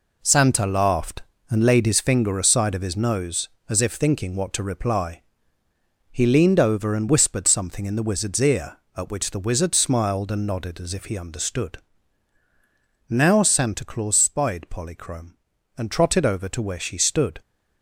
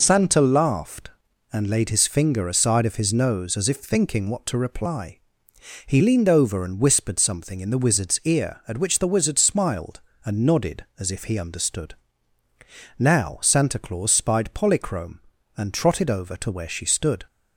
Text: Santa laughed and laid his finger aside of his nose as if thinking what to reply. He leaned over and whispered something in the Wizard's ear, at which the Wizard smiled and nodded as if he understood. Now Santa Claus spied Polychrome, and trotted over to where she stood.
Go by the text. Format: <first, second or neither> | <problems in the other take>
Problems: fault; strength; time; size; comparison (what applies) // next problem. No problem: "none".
second | gets quieter; strong; throughout; 8 dB